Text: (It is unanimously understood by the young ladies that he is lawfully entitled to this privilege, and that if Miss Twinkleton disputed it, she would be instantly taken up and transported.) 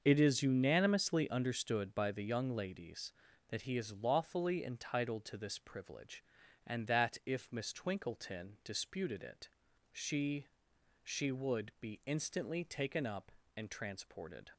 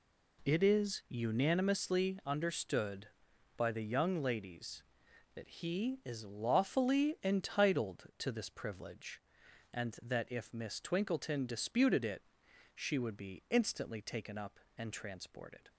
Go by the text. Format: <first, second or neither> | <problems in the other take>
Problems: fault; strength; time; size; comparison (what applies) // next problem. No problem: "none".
second | starts louder than the rest; until 1.0 s; 6.5 dB // says "she" twice; at 11.0 s